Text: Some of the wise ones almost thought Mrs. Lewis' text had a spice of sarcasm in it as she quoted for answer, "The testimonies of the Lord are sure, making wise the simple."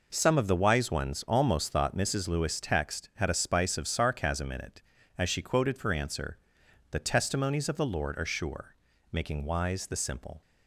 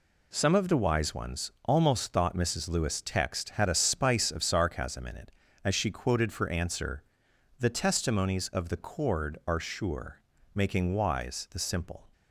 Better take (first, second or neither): first